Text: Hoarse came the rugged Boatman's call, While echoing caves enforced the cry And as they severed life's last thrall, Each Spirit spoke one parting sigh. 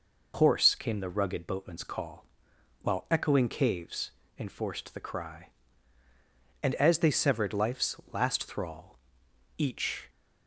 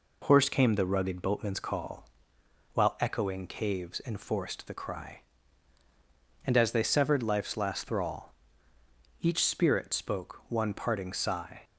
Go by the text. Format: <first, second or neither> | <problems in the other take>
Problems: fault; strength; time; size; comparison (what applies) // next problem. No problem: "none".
second | pauses between "caves" and "enforced"; slight; at 4.1 s; 0.26 s long // pauses between "life's" and "last"; slight; at 7.9 s; 0.16 s long // stops before "Spirit spoke one parting sigh"; at 10.0 s